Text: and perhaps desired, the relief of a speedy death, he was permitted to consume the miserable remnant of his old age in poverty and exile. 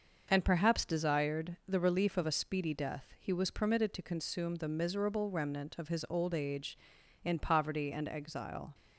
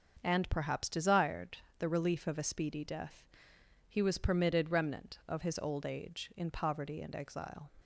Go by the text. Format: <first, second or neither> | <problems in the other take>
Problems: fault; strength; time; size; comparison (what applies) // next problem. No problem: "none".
first | starts louder than the rest; until 1.2 s; 6.5 dB; also in the first // skips "to consume the miserable"; at 4.6 s